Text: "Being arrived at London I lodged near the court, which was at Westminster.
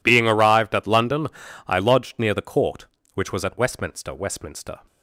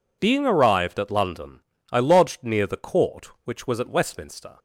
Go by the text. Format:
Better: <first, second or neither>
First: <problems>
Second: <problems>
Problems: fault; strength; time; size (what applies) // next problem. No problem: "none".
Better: second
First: pauses between "London" and "I"; at 1.2 s; 0.40 s long // says "Westminster" twice; at 4.1 s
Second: pauses between "London" and "I"; slight; at 1.6 s; 0.32 s long